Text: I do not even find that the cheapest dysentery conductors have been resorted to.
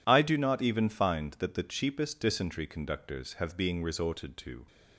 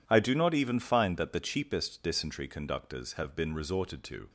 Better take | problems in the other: second | says "being" for "been"; at 3.5 s

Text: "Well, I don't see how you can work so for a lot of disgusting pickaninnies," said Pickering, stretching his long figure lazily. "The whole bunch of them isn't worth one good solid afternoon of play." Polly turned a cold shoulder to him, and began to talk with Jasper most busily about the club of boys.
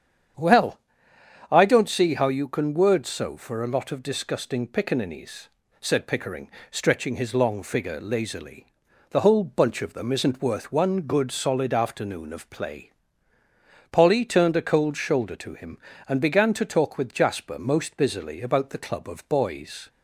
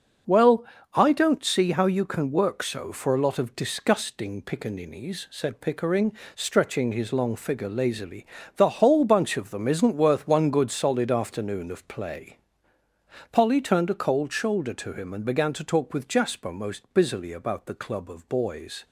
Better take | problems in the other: second | starts louder than the rest; strong; until 2.0 s; 8.5 dB; also in the second // says "word" for "work"; at 2.7 s

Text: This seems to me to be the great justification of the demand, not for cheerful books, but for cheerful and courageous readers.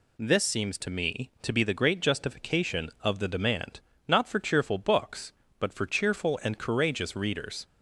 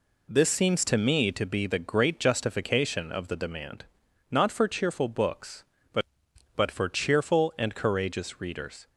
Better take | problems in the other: first | says "but" twice; at 6.5 s

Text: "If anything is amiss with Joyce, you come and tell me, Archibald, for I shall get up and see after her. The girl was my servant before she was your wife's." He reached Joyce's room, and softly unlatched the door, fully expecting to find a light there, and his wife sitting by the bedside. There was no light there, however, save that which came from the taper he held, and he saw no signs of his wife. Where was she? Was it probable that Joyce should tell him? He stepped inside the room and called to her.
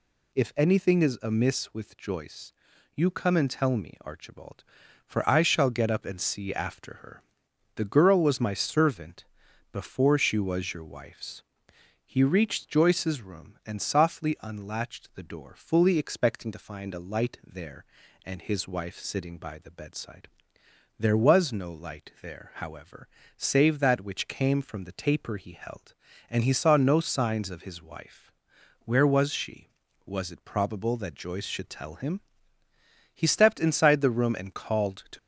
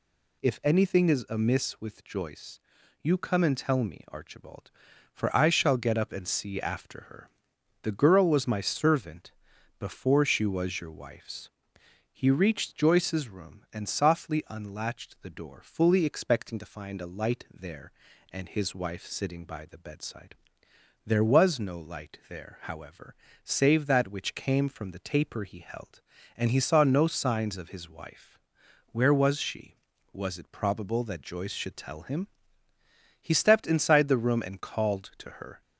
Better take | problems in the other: second | pauses between "servant" and "before"; noticeable; at 9.2 s; 0.48 s long; noticeable in the second // stops before "her"; at 35.1 s

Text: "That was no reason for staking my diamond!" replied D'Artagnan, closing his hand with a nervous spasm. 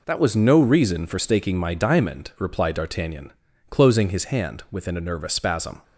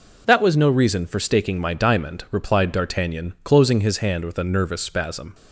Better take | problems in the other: second | says "within" for "with"; at 4.7 s

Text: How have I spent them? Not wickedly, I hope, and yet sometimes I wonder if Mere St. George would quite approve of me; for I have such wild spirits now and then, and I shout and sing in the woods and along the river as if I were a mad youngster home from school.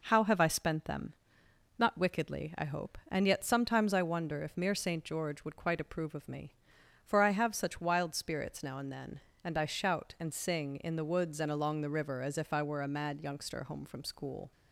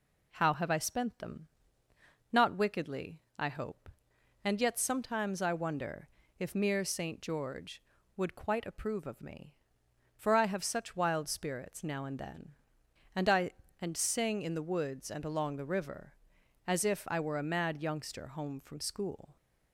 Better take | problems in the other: first | pauses between "wonder" and "if"; slight; at 6.0 s; 0.30 s long // skips "shout"; at 13.6 s

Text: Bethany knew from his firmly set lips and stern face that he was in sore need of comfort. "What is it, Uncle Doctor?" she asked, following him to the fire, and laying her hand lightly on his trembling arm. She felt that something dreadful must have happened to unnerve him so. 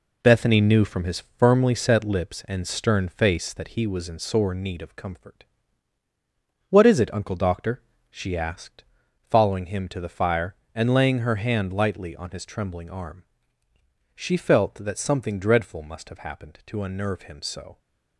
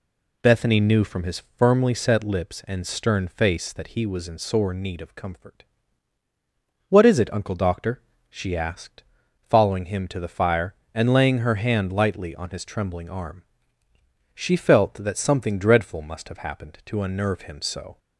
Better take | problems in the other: second | gets quieter; strong; throughout; 7 dB // pauses between "his" and "firmly"; slight; at 1.2 s; 0.16 s long; slight in the second

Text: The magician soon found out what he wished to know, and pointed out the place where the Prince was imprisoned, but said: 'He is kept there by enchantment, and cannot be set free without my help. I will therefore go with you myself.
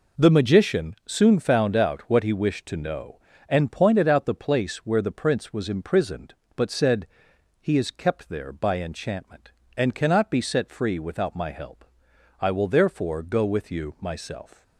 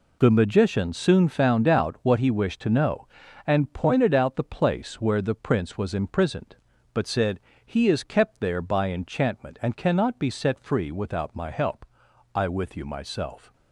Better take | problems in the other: first | skips "will therefore go"; at 12.4 s

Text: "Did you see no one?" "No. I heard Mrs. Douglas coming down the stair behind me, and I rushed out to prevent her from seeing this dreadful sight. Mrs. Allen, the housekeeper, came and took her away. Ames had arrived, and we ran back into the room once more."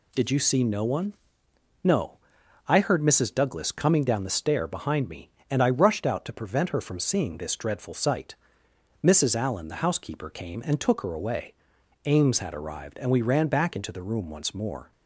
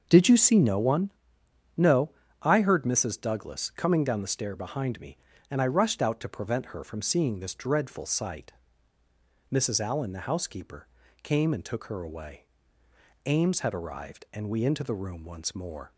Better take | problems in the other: first | starts louder than the rest; until 1.1 s; 6.5 dB // skips "ran back"; at 14.6 s

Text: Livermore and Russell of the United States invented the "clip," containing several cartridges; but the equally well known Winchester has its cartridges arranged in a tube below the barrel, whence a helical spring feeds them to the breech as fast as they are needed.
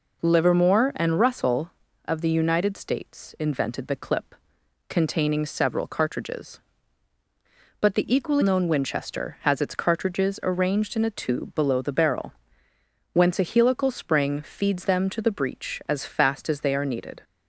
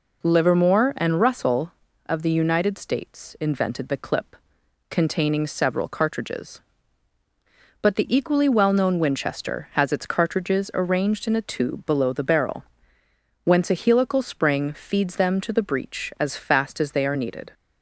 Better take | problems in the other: second | skips "well"; at 8.4 s

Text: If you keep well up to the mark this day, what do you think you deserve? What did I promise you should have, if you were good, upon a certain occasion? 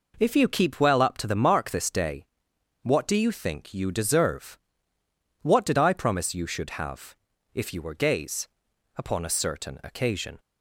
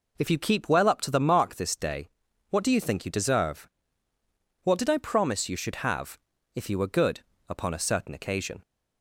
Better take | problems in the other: second | says "gays" for "good"; at 7.9 s

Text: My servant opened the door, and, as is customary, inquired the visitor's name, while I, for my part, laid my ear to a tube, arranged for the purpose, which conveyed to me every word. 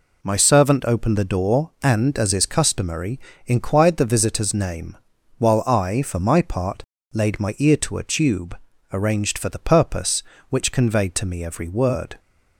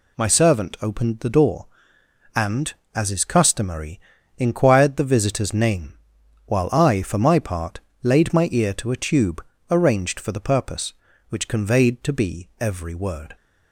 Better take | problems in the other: first | says "be" for "me"; at 12.1 s

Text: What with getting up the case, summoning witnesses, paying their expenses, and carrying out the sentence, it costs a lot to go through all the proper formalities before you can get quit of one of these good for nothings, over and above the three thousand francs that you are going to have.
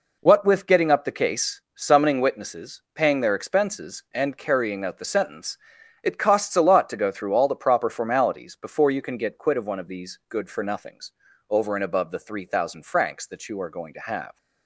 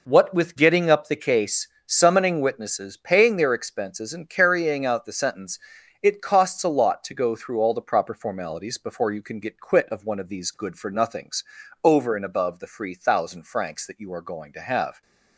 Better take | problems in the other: first | says "free" for "three"; at 12.6 s

